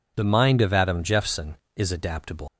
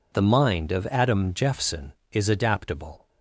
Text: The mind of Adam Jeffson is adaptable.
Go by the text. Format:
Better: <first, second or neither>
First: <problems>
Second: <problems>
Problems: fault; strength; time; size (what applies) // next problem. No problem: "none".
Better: second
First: leaves "adaptable" unfinished; at 2.4 s; 125 ms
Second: none